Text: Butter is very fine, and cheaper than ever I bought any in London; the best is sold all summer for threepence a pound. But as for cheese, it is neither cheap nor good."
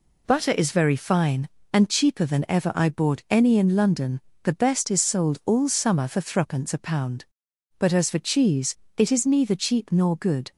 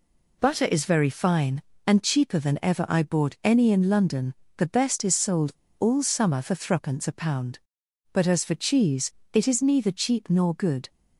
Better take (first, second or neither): first